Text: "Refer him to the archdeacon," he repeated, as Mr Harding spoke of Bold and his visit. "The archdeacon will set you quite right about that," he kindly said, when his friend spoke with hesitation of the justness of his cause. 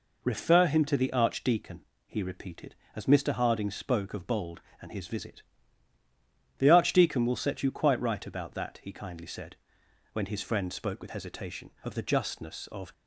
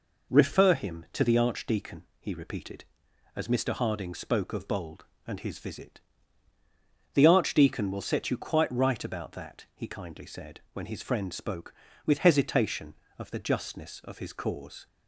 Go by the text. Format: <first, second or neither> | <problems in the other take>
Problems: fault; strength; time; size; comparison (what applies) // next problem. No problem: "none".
second | stops before "his cause"; at 12.9 s